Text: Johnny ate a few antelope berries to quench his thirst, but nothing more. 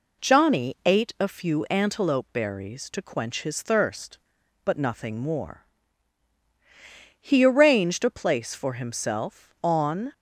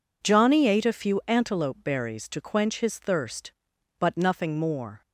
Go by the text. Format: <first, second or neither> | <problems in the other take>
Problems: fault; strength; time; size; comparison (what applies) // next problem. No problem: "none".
second | goes on to say "He arranged a place for himself on"; strong; from 7.2 s on; 2.9 s long